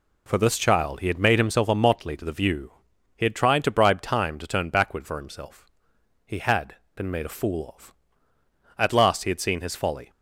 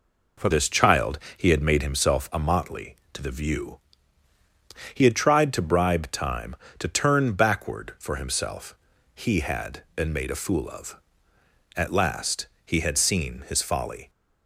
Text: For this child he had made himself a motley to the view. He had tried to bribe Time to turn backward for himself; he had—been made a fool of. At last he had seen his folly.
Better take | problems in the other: first | changes voice at "this"; from 0.5 s on; 13.5 s long // pauses between "child" and "he"; slight; at 1.1 s; 0.18 s long // pauses between "last" and "he"; slight; at 12.4 s; 0.18 s long

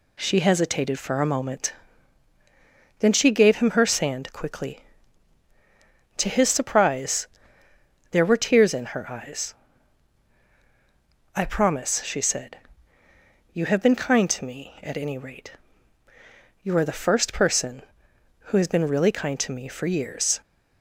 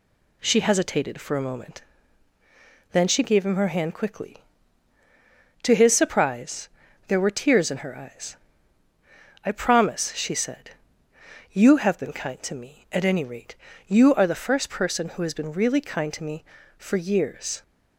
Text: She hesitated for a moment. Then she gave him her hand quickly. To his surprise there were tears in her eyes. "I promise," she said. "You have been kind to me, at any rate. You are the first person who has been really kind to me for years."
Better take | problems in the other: second | says "sand" for "hand"; at 3.8 s // pauses between "surprise" and "there"; noticeable; at 7.2 s; 0.82 s long; also in the second

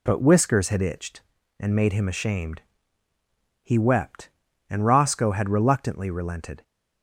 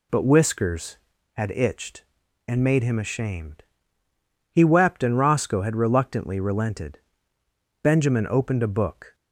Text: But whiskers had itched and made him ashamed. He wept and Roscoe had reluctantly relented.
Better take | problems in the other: first | goes on to say "Benjamin opened a book"; from 7.8 s on; 1.3 s long

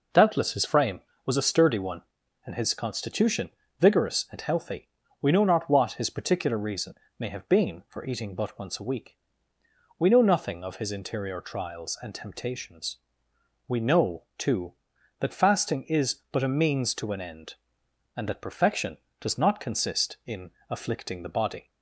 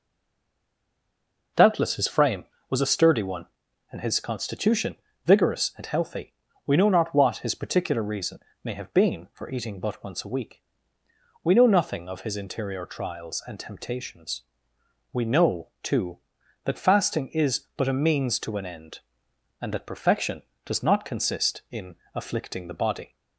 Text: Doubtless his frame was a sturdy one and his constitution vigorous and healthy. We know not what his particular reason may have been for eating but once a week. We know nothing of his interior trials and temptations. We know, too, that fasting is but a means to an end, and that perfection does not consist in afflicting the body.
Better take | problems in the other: first | stays silent before the first word; noticeable; until 1.5 s; 1.5 s long // pauses between "constitution" and "vigorous"; slight; at 4.9 s; 0.30 s long; slight in the first // pauses between "reason" and "may"; slight; at 8.3 s; 0.24 s long; slight in the first // pauses between "in" and "afflicting"; slight; at 21.9 s; 0.20 s long; slight in the first

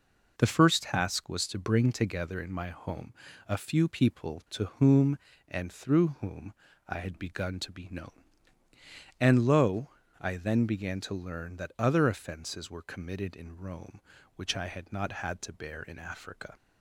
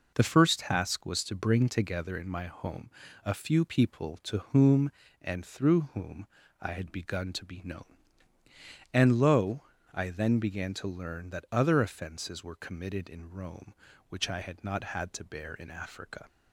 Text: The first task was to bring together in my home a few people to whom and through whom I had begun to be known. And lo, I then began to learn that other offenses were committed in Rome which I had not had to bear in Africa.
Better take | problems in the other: neither | pauses between "home" and "a"; slight; the same in both // pauses between "whom" and "I"; slight; the same in both

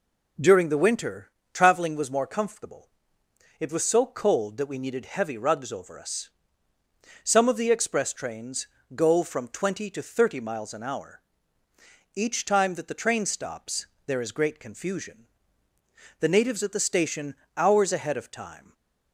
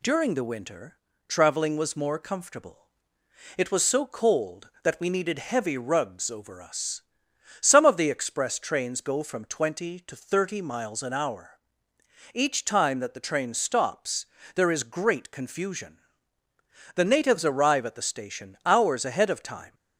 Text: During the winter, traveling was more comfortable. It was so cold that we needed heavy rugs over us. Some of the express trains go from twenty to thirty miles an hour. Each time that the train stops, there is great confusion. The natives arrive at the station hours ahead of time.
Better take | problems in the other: second | pauses between "trains" and "go"; slight; at 8.6 s; 0.28 s long // skips "arrive"; at 16.6 s // pauses between "station" and "hours"; slight; at 17.3 s; 0.22 s long // stays silent after the last word; slight; from 18.6 s on; 0.5 s long

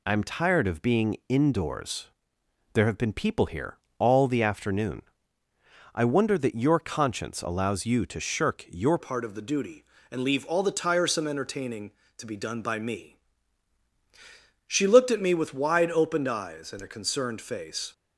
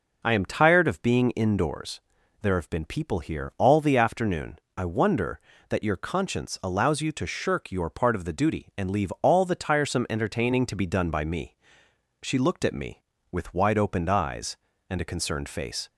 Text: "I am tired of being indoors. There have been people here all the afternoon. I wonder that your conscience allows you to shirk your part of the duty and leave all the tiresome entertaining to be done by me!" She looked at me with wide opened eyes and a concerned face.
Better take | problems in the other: second | pauses between "here" and "all"; slight; at 3.7 s; 0.22 s long // changes voice at "part"; from 8.9 s on; 9.0 s long

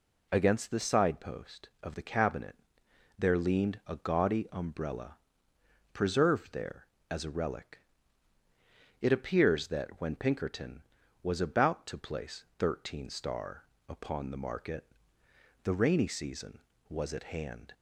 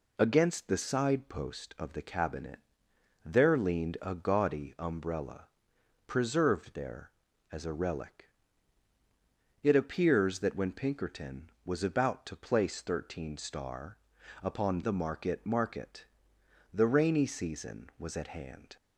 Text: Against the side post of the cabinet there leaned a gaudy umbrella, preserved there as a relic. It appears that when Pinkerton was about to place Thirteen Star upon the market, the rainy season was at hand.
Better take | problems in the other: first | pauses between "cabinet" and "there"; noticeable; at 2.5 s; 0.66 s long; noticeable in the first // pauses between "Star" and "upon"; at 13.9 s; 0.44 s long; slight in the first // says "market" twice; at 15.4 s

